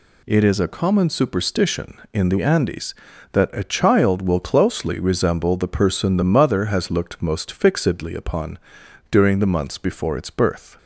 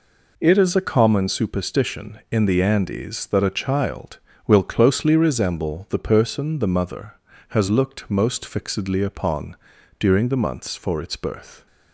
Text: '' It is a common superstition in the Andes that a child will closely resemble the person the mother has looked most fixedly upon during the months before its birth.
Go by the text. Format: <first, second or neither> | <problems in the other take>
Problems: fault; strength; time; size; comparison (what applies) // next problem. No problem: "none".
first | pauses between "upon" and "during"; at 9.5 s; 0.44 s long; noticeable in the first // says "for" for "before"; at 10.7 s